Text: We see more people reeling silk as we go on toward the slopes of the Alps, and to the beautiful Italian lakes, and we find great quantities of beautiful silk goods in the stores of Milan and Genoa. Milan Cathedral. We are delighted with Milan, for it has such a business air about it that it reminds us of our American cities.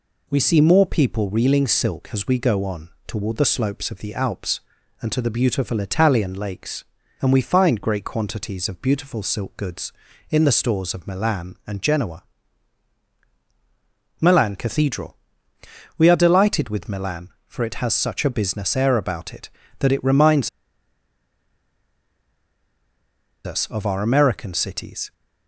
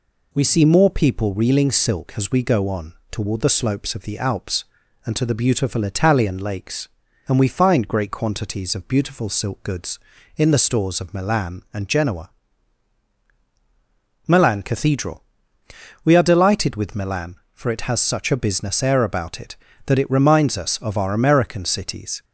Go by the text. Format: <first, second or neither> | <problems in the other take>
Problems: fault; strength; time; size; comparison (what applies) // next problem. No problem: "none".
second | pauses between "on" and "toward"; slight; at 2.8 s; 0.16 s long; slight in the second // pauses between "reminds" and "us"; strong; at 20.4 s; 2.9 s long